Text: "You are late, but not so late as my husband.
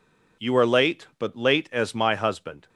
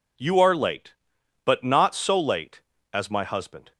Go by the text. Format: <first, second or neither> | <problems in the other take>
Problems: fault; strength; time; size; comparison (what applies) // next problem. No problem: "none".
second | skips "not so"; at 1.3 s